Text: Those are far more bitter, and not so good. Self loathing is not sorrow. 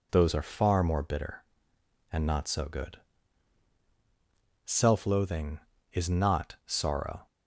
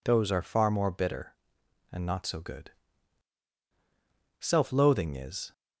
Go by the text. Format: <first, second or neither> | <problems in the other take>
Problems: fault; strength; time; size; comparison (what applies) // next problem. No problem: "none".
first | stops before "not sorrow"; at 5.5 s